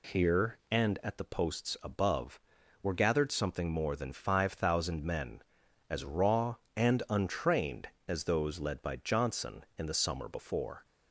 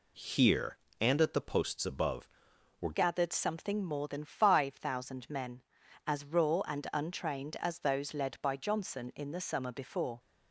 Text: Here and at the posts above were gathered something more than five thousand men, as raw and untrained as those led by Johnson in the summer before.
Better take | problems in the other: first | changes voice at "gathered"; from 2.9 s on; 7.2 s long

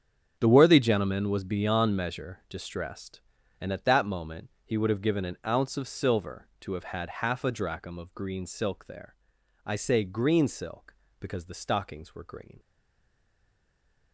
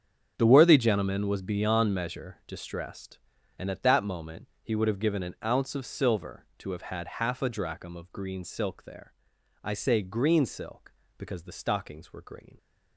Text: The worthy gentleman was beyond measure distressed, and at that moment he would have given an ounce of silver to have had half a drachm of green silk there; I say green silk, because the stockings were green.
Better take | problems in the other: second | starts louder than the rest; strong; until 1.4 s; 7.5 dB; strong in the second // stays silent after the last word; noticeable; from 12.5 s on; 1.6 s long

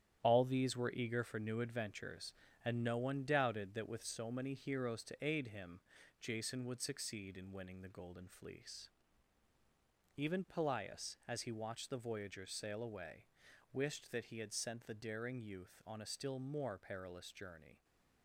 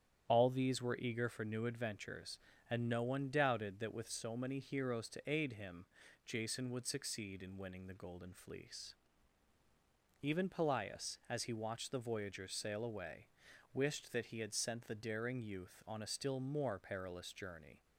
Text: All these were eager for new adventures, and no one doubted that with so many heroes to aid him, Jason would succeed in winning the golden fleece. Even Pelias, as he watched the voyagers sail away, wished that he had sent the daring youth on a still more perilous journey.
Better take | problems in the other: second | gets quieter; strong; throughout; 7.5 dB // starts louder than the rest; strong; until 1.2 s; 10.5 dB; strong in the second

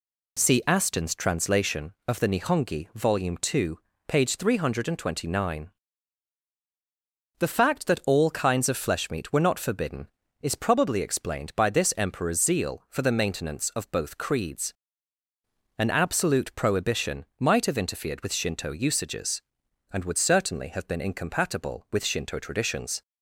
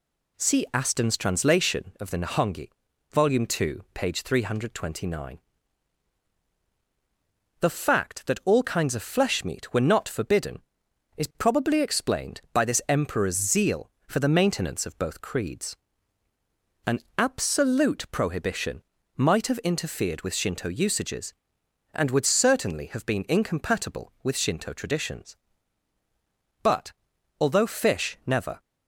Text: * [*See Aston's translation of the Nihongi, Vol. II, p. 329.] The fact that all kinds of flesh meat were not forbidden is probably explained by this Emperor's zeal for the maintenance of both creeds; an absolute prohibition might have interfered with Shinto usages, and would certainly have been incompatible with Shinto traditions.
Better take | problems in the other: first | pauses between "an" and "absolute"; slight; at 17.0 s; 0.18 s long // pauses between "prohibition" and "might"; slight; at 18.8 s; 0.34 s long // goes on to say "But although fish never"; strong; from 26.6 s on; 1.9 s long

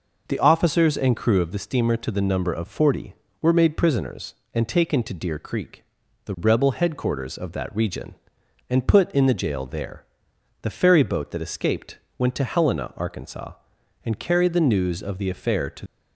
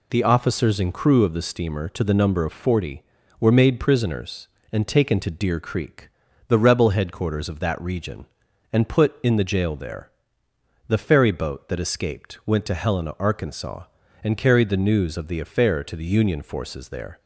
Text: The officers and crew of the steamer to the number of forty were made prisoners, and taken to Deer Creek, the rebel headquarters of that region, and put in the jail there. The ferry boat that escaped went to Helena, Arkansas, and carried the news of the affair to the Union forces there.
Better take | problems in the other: second | pauses between "escaped" and "went"; slight; at 11.9 s; 0.20 s long // stops before "the Union forces there"; at 15.8 s

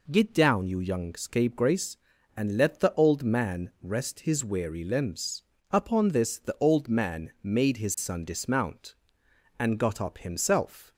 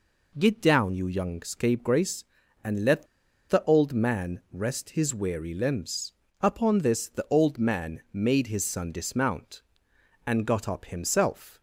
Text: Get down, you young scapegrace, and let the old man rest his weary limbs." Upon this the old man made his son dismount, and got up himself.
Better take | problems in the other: first | pauses between "let" and "the"; at 3.0 s; 0.43 s long

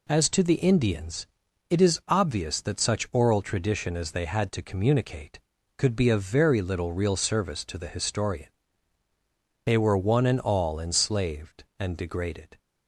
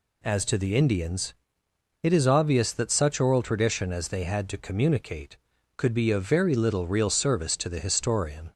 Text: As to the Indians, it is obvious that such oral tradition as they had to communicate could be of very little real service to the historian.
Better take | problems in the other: second | goes on to say "They were one and all enslaved and degraded"; strong; from 9.6 s on; 2.9 s long

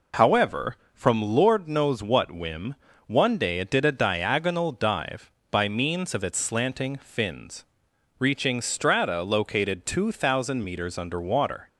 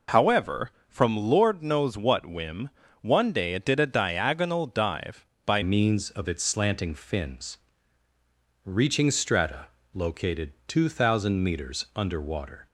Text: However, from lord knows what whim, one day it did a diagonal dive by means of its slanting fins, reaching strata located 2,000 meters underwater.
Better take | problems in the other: first | changes voice at "means"; from 5.6 s on; 7.0 s long // pauses between "strata" and "located"; slight; at 9.6 s; 0.30 s long

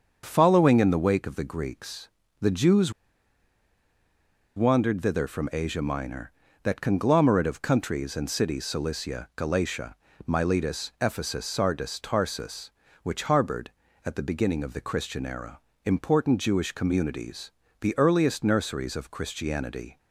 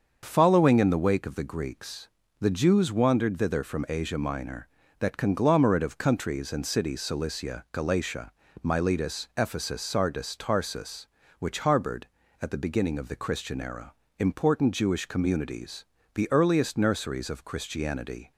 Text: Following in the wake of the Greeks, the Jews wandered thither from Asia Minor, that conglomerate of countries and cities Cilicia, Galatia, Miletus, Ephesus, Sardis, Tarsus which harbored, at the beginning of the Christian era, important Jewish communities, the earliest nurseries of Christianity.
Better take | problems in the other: second | starts louder than the rest; until 1.2 s; 6.5 dB; also in the second // pauses between "Jews" and "wandered"; strong; at 2.9 s; 1.6 s long

